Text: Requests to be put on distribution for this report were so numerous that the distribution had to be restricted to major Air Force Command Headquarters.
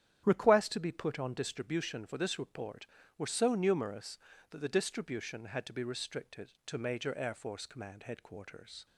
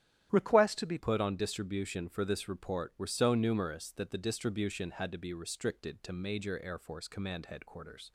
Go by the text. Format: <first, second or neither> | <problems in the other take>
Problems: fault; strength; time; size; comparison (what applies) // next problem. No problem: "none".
first | starts louder than the rest; strong; until 1.3 s; 11 dB; strong in the first // changes voice at "put"; from 0.9 s on; 7.2 s long